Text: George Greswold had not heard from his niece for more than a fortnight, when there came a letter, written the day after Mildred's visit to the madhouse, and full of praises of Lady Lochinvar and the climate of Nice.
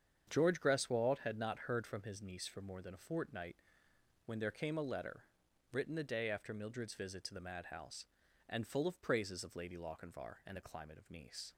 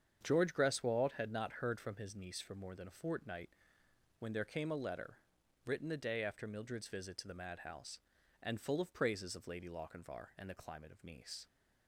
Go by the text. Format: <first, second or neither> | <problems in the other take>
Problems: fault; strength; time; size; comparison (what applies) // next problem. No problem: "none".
neither | starts louder than the rest; strong; the same in both